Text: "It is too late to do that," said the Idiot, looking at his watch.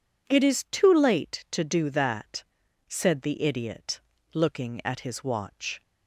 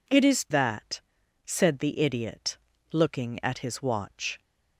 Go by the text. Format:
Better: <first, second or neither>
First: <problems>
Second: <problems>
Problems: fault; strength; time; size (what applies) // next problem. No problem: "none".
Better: first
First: none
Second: skips "too late to do"; at 0.4 s